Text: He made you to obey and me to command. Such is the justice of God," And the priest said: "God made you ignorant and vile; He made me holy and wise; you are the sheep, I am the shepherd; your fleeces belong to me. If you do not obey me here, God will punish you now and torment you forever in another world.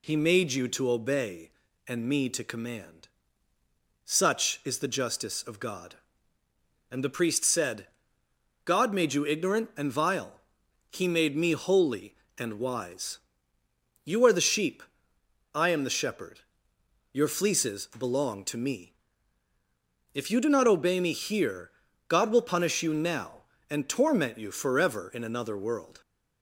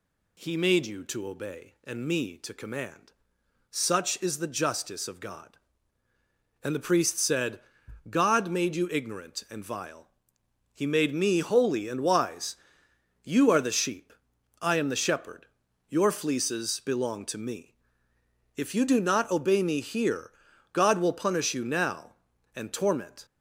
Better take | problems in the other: first | stops before "you forever in another world"; at 23.2 s

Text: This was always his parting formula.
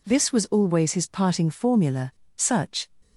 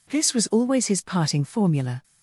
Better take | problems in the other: second | goes on to say "Such"; from 2.3 s on; 0.54 s long

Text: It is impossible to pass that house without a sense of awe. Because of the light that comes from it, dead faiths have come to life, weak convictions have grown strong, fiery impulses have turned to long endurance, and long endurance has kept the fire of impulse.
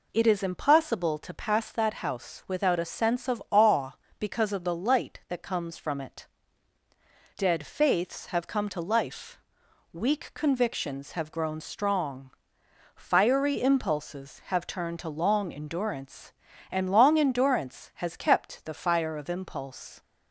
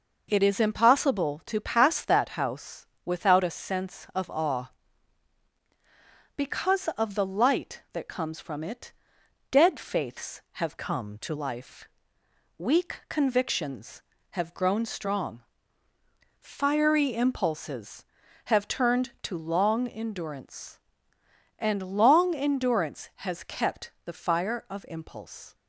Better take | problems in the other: first | pauses between "house" and "without"; slight; at 2.8 s; 0.18 s long // changes voice from "come" to "to"; from 10.7 to 11.3 s; 0.6 s long

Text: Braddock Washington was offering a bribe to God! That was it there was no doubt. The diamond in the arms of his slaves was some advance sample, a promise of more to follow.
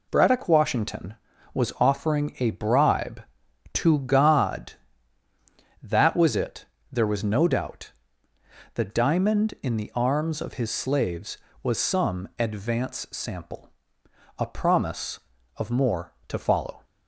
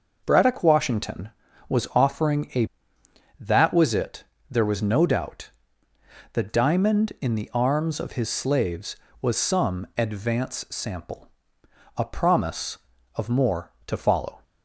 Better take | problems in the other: first | skips "bribe to God"; at 3.0 s // pauses between "it" and "there"; slight; at 4.2 s; 0.26 s long; slight in the first

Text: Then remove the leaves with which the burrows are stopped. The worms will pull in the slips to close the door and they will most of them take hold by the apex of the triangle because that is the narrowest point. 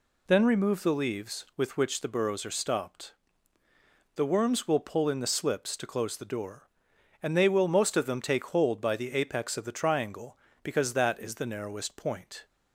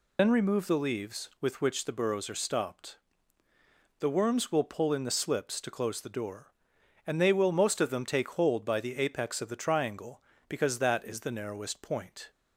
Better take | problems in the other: first | loses the start of "Then"; at 0.1 s; 60 ms

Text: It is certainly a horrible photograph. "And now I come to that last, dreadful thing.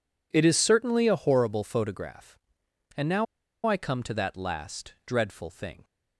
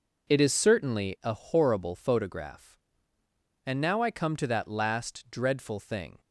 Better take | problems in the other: second | pauses between "now" and "I"; at 3.2 s; 0.40 s long

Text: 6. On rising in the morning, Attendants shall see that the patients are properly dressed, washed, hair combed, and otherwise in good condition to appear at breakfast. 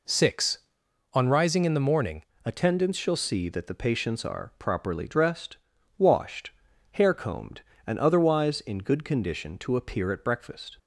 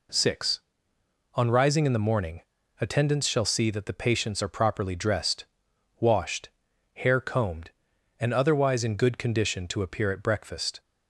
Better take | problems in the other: second | changes voice at "Attendants"; from 2.4 s on; 8.3 s long

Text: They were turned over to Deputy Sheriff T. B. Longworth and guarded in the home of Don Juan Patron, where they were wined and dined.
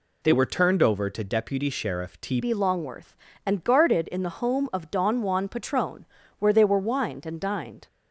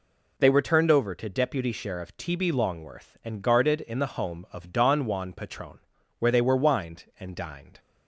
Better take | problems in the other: second | changes voice at "B"; from 2.3 s on; 5.5 s long

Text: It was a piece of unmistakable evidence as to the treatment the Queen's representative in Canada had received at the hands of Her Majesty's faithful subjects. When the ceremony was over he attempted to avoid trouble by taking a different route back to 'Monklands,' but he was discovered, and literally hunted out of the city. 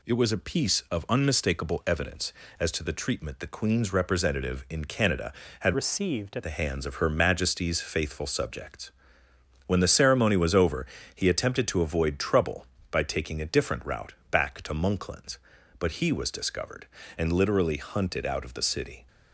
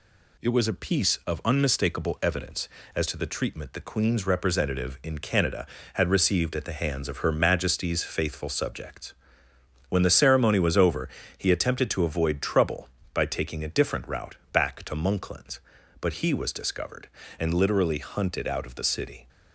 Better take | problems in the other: second | changes voice from "received" to "at"; from 5.7 to 6.4 s; 0.7 s long // pauses between "over" and "he"; slight; at 10.8 s; 0.30 s long; slight in the second // pauses between "route" and "back"; slight; at 14.1 s; 0.16 s long; slight in the second

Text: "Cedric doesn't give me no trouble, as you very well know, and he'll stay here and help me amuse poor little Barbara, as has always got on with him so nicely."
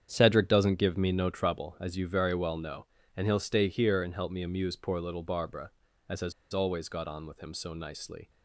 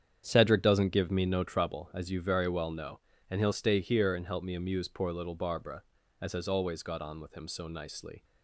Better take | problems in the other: second | starts louder than the rest; strong; until 1.1 s; 8.5 dB; strong in the second // pauses between "has" and "always"; slight; at 6.3 s; 0.20 s long

